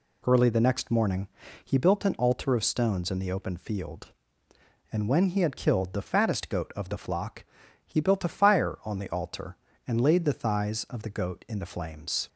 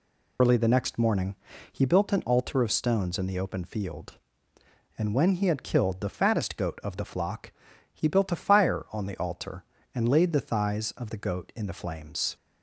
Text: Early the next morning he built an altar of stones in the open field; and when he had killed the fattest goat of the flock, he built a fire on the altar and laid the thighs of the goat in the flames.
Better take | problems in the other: first | loses the start of "Early"; at 0.3 s; 90 ms // pauses between "morning" and "he"; slight; at 1.3 s; 0.36 s long; slight in the first

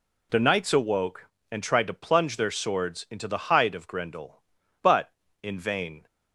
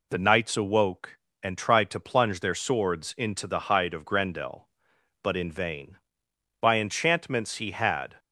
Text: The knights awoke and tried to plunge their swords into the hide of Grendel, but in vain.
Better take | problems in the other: first | goes on to say "By enchantments he had"; from 6.6 s on; 1.5 s long

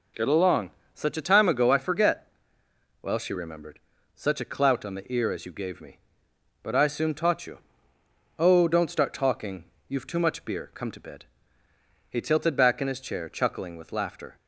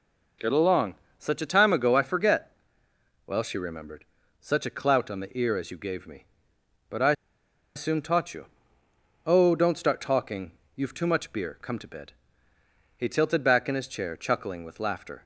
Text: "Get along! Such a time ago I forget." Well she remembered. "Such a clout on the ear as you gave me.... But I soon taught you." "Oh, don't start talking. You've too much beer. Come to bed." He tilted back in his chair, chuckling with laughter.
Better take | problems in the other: first | pauses between "I" and "soon"; noticeable; at 7.1 s; 0.61 s long

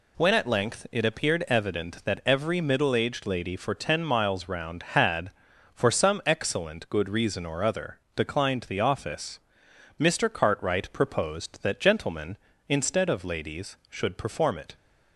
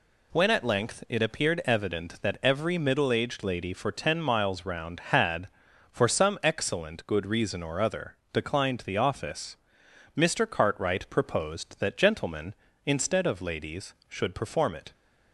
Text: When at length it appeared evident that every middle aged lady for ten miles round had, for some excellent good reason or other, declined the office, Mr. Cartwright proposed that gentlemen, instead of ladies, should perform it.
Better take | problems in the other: neither | none

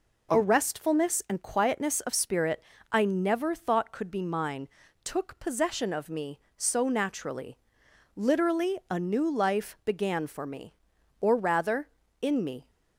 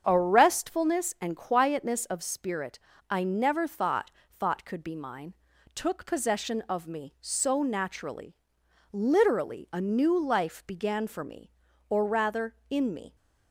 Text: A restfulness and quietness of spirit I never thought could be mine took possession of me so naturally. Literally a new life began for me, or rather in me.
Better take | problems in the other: first | starts louder than the rest; strong; until 1.0 s; 7 dB // pauses between "spirit" and "I"; slight; at 2.7 s; 0.32 s long; slight in the first // says "thought" twice; at 4.3 s // pauses between "mine" and "took"; at 5.3 s; 0.40 s long; slight in the first

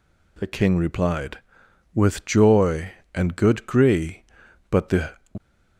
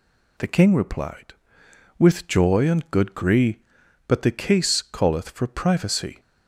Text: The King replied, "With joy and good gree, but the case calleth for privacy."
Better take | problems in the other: second | stops before "case calleth for privacy"; at 5.3 s

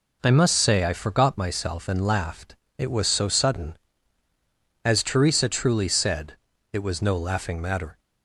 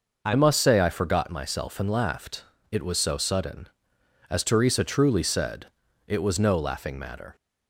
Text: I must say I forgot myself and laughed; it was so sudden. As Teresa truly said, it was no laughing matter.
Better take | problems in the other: first | changes voice at "must"; from 0.3 s on; 7.0 s long

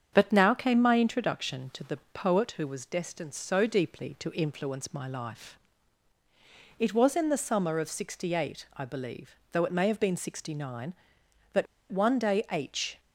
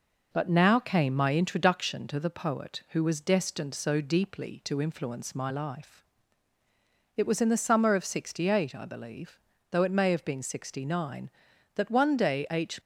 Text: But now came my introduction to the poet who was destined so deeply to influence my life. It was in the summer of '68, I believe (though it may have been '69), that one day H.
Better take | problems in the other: second | starts louder than the rest; strong; until 1.1 s; 7.5 dB // pauses between "the" and "poet"; slight; at 1.9 s; 0.16 s long // pauses between "that" and "one"; slight; at 11.6 s; 0.25 s long

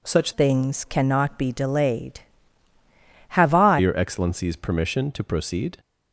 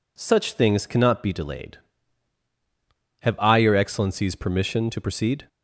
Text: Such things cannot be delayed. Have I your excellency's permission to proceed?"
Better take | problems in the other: second | changes voice from "things" to "I"; from 0.3 to 3.7 s; 3.4 s long

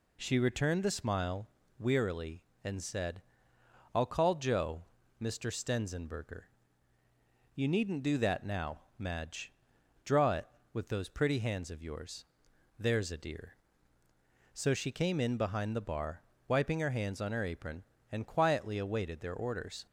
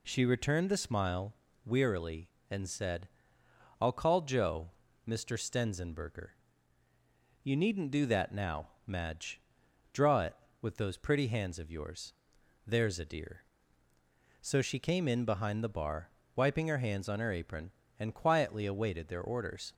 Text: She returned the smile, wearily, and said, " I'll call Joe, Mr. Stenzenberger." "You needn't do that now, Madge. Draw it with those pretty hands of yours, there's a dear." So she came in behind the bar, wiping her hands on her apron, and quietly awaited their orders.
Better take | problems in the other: neither | none

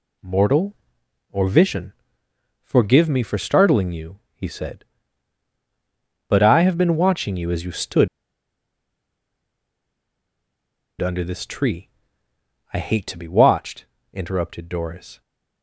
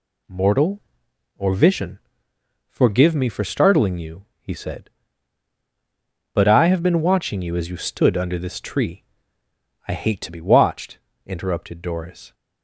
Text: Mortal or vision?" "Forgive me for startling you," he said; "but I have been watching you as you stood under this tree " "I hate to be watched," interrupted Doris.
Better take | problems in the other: second | pauses between "stood" and "under"; strong; at 8.0 s; 2.9 s long

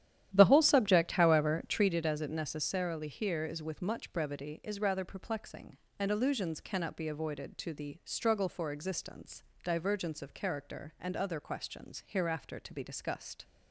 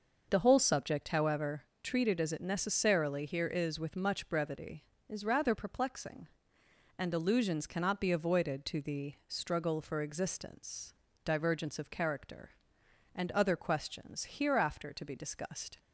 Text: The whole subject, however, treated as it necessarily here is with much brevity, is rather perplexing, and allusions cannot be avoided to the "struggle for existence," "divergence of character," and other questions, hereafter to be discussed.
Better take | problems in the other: second | starts louder than the rest; strong; until 2.0 s; 11.5 dB

